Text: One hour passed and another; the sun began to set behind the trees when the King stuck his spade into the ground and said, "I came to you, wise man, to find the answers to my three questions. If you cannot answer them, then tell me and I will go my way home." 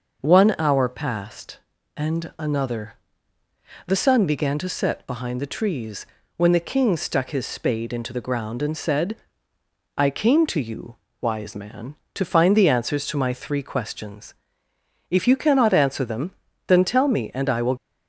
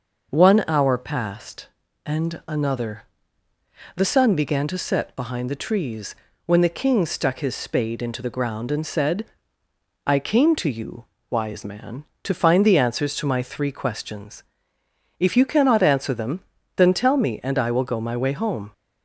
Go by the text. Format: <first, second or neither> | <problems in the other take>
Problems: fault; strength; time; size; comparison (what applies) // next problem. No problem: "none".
second | pauses between "trees" and "when"; slight; at 6.0 s; 0.30 s long; slight in the second // stops before "go my way home"; at 17.7 s